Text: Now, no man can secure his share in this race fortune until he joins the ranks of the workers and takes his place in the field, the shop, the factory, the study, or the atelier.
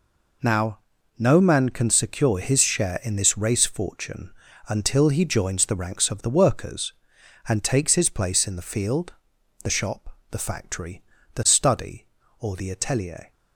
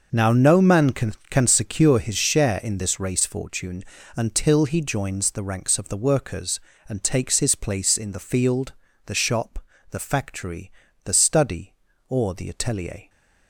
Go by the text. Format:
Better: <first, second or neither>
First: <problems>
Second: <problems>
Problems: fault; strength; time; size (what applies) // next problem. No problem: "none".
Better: first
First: pauses between "fortune" and "until"; at 4.3 s; 0.38 s long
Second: says "can" twice; at 1.2 s // pauses between "fortune" and "until"; slight; at 3.8 s; 0.32 s long